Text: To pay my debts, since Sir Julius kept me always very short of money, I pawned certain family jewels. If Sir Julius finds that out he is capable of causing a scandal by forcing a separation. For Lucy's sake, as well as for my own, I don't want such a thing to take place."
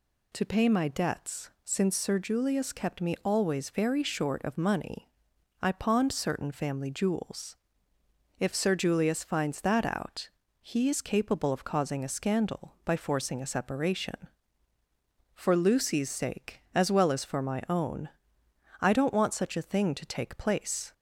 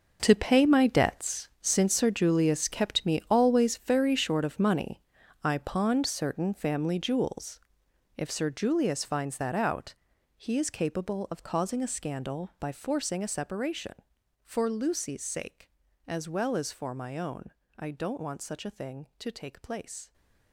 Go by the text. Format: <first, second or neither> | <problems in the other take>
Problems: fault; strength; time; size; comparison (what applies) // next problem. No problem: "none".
first | gets quieter; strong; throughout; 13.5 dB // pauses between "out" and "he"; at 9.9 s; 0.42 s long; slight in the first